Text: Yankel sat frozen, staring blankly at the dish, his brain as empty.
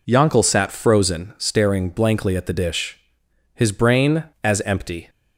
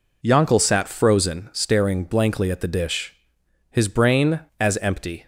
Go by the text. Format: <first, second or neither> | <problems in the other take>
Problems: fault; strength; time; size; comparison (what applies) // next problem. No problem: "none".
neither | none